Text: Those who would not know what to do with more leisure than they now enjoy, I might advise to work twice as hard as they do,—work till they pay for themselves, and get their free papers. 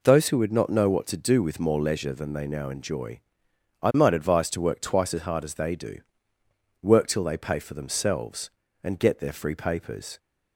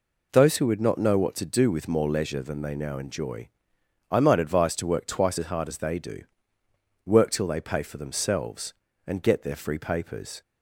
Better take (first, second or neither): neither